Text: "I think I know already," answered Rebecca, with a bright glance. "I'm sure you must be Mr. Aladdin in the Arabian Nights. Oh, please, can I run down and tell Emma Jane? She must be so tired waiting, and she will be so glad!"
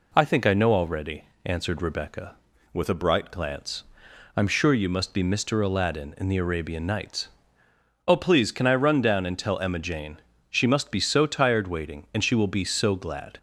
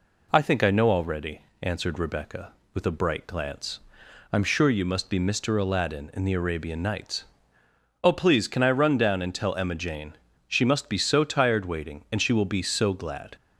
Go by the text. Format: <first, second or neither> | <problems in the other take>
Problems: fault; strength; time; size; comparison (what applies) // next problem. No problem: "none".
second | changes voice from "with" to "bright"; from 2.7 to 3.3 s; 0.6 s long